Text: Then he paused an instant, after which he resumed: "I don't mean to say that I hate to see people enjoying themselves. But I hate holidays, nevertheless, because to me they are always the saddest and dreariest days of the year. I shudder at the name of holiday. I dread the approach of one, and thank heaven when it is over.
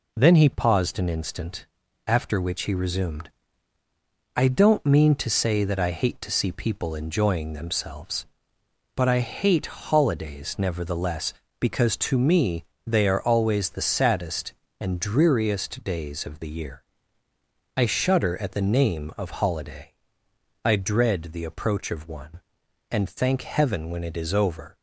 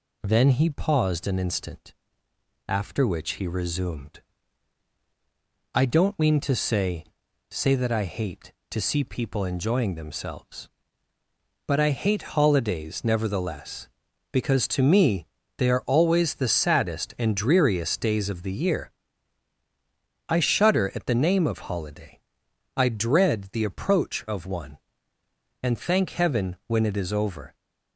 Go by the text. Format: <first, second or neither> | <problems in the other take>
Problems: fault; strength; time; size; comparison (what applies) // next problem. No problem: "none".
first | says "say" twice; at 7.4 s // pauses between "me" and "they"; slight; at 15.2 s; 0.30 s long; slight in the first